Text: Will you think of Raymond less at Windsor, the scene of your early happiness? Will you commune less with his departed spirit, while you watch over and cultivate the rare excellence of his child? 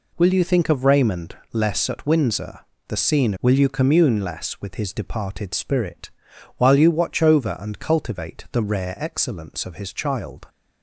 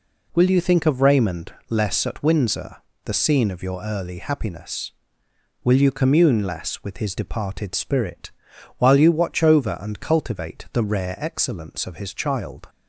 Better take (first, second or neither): second